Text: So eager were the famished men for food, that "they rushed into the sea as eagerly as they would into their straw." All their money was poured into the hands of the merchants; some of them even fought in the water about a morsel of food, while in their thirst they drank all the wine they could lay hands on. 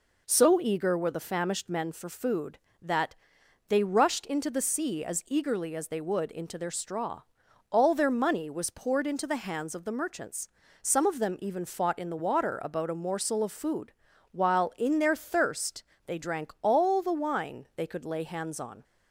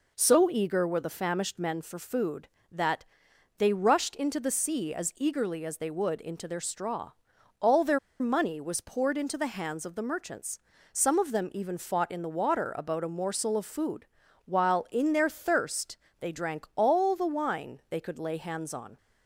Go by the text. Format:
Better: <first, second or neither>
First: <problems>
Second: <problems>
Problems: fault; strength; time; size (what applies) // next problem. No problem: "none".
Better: first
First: pauses between "that" and "they"; noticeable; at 3.1 s; 0.54 s long // pauses between "thirst" and "they"; slight; at 15.8 s; 0.24 s long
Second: pauses between "that" and "they"; noticeable; at 3.0 s; 0.54 s long // pauses between "their" and "money"; slight; at 7.9 s; 0.21 s long // pauses between "thirst" and "they"; slight; at 15.9 s; 0.24 s long